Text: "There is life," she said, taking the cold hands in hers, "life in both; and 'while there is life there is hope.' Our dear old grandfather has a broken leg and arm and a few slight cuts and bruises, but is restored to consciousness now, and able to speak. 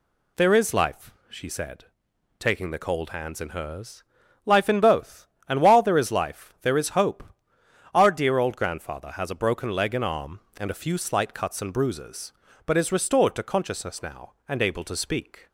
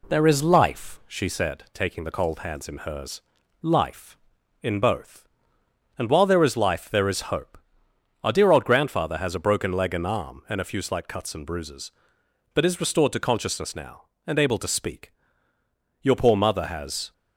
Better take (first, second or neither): first